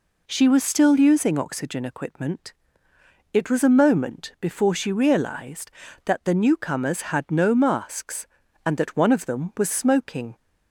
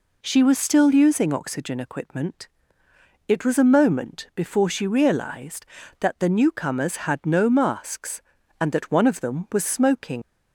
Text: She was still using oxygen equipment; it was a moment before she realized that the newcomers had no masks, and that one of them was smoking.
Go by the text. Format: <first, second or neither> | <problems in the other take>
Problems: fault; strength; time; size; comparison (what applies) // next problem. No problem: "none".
first | leaves "smoking" unfinished; at 10.2 s; 75 ms